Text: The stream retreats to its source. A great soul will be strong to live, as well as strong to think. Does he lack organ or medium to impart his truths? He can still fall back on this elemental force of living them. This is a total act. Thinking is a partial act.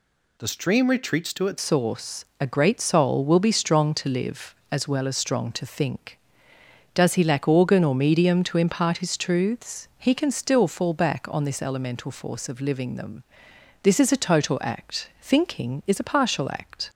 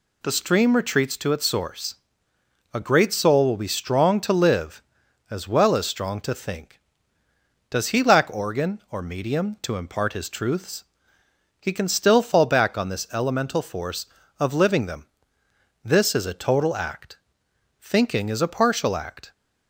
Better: second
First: changes voice at "source"; from 1.5 s on; 15.3 s long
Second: none

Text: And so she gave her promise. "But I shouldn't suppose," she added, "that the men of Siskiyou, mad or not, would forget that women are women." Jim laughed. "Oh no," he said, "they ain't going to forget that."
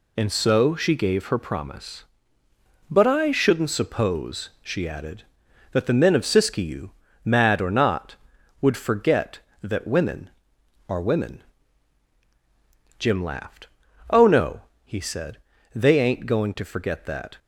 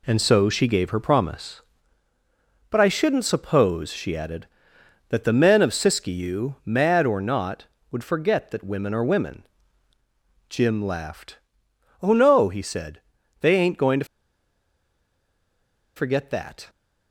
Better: first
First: none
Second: pauses between "to" and "forget"; strong; at 14.0 s; 1.9 s long

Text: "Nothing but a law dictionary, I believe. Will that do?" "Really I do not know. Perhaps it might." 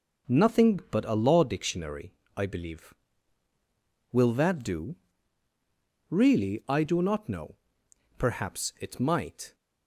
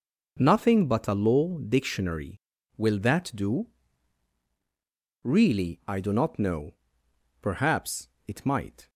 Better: first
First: none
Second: skips "I believe"; at 2.5 s // pauses between "Perhaps" and "it"; slight; at 8.0 s; 0.18 s long

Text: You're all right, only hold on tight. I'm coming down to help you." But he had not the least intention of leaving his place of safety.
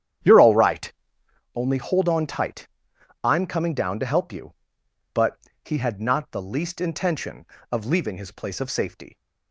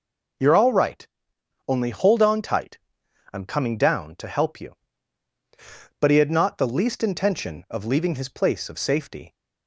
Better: second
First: starts louder than the rest; strong; until 1.4 s; 9.5 dB // pauses between "But" and "he"; slight; at 5.3 s; 0.26 s long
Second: none

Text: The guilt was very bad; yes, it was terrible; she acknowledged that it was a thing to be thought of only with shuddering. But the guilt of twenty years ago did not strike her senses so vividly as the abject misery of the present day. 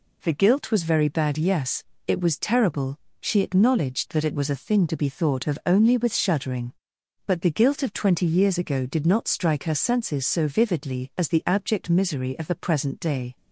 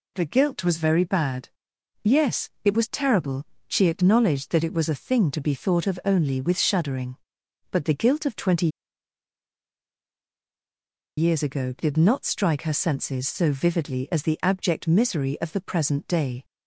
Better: first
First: none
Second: pauses between "twenty" and "years"; strong; at 8.6 s; 2.4 s long

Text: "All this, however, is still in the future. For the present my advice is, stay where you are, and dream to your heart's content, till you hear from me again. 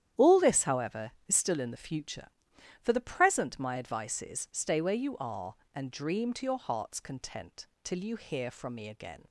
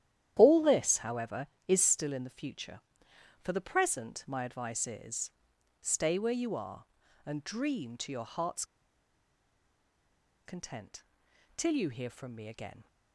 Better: first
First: starts louder than the rest; strong; until 1.3 s; 10.5 dB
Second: starts louder than the rest; strong; until 1.3 s; 11 dB // pauses between "heart's" and "content"; strong; at 8.6 s; 1.8 s long

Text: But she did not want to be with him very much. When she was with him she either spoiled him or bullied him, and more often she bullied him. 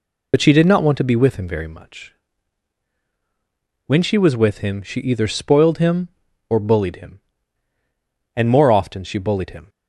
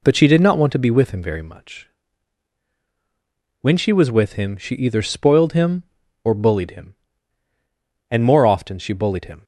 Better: second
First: loses the start of "But"; at 0.3 s; 50 ms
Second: none

